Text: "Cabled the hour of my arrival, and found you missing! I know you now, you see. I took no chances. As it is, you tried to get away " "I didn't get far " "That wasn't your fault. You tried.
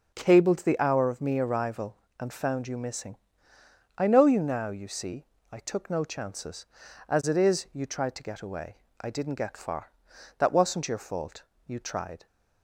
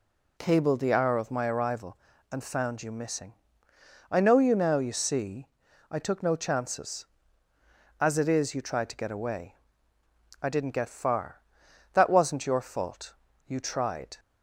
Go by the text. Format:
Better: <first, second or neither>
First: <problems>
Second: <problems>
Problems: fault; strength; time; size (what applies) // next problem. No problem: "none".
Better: second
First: starts louder than the rest; until 1.1 s; 7 dB // says "me" for "my"; at 1.2 s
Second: none